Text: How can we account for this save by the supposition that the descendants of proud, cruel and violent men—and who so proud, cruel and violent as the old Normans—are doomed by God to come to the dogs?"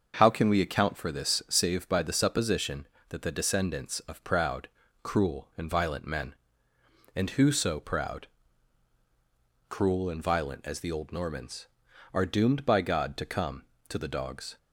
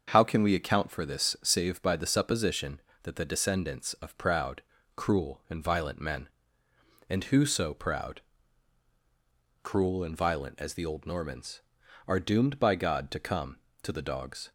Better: neither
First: starts louder than the rest; until 1.1 s; 6.5 dB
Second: starts louder than the rest; until 1.0 s; 6.5 dB

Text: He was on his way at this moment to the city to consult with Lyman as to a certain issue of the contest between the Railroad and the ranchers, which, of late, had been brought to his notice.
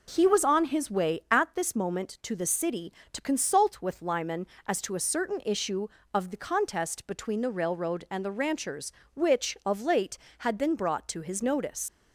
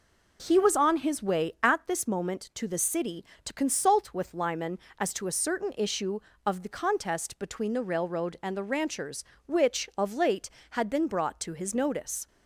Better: second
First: leaves "notice" unfinished; at 11.8 s; 65 ms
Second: none

